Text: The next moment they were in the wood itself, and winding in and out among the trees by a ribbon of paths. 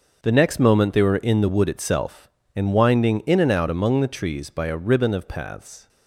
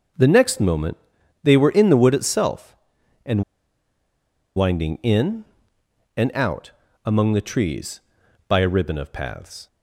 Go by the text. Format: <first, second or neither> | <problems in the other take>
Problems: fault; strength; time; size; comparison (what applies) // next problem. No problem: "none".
first | starts louder than the rest; until 1.6 s; 6 dB; also in the first // pauses between "moment" and "they"; noticeable; at 0.9 s; 0.46 s long // pauses between "and" and "winding"; at 3.4 s; 1.1 s long // pauses between "out" and "among"; slight; at 6.7 s; 0.34 s long